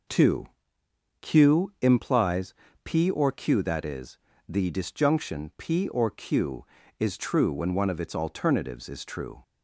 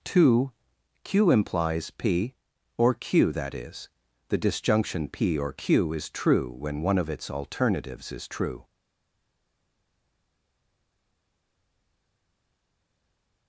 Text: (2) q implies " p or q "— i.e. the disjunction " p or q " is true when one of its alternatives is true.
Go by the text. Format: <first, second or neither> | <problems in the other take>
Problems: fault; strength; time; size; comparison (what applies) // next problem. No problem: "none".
first | stays silent after the last word; strong; from 8.6 s on; 4.8 s long